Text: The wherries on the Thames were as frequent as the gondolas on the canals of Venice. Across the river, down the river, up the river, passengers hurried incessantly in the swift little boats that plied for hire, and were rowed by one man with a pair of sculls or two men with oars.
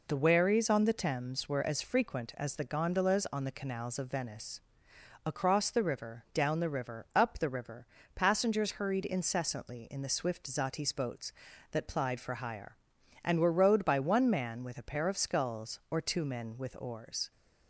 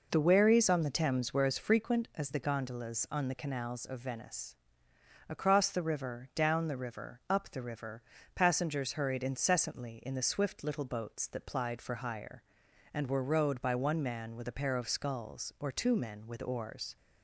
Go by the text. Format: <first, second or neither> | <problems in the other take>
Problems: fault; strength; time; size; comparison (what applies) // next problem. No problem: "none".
second | says "zatis" for "little"; at 10.4 s